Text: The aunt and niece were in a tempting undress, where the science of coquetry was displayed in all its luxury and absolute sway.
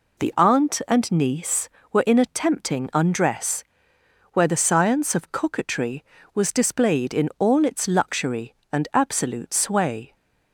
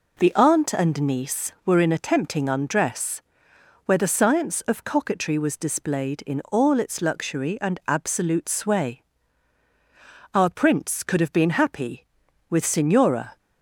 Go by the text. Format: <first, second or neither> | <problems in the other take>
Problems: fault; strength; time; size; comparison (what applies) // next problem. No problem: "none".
first | goes on to say "Our prince could have been happy with Signora"; strong; from 10.3 s on; 3.0 s long